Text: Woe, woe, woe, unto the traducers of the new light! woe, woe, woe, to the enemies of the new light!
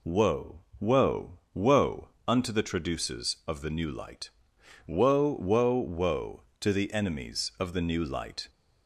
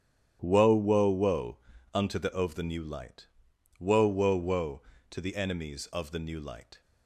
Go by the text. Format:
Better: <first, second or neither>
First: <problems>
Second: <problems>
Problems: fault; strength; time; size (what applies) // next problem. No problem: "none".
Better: first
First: none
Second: starts louder than the rest; strong; until 1.4 s; 10 dB // skips "traducers"; at 2.3 s